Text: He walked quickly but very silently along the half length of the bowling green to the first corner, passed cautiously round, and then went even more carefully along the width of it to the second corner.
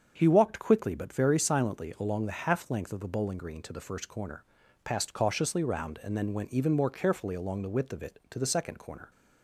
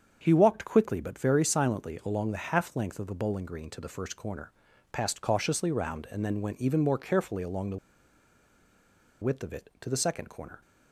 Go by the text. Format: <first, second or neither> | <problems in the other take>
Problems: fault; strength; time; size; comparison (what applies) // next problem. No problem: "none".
first | starts louder than the rest; until 1.2 s; 7 dB; also in the first // pauses between "the" and "width"; strong; at 7.7 s; 1.4 s long